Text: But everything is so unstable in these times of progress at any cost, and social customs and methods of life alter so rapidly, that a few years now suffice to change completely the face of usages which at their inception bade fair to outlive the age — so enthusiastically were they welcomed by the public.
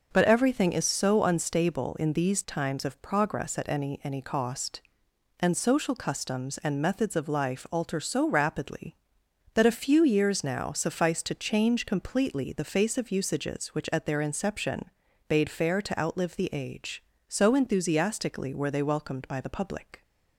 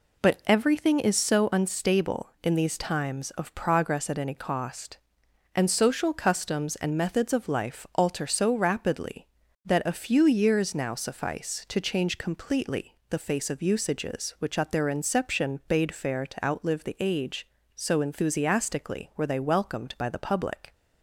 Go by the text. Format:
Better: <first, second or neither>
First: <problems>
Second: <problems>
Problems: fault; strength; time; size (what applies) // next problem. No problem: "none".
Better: second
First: says "any" twice; at 4.0 s // pauses between "inception" and "bade"; at 14.8 s; 0.42 s long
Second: none